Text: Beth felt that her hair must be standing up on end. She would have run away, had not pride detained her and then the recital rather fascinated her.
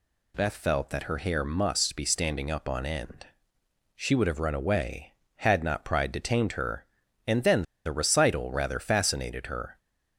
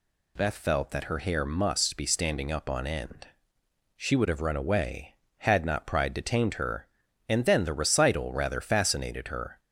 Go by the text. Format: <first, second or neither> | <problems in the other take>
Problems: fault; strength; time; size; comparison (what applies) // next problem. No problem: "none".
second | pauses between "then" and "the"; slight; at 7.6 s; 0.22 s long